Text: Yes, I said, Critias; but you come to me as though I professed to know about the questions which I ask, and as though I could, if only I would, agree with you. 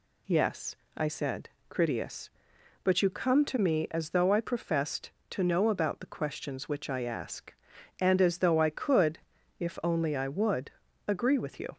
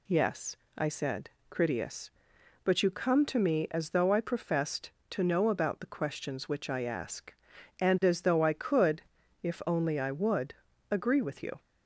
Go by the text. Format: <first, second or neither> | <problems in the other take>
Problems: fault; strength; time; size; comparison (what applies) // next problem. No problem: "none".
neither | none